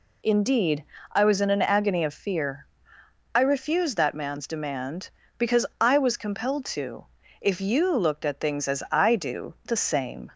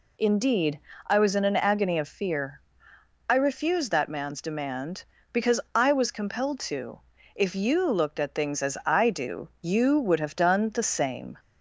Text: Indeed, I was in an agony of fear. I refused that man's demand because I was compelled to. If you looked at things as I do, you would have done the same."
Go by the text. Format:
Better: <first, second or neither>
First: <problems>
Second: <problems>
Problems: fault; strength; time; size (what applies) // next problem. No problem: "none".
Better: second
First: skips "you would have done"; at 9.5 s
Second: none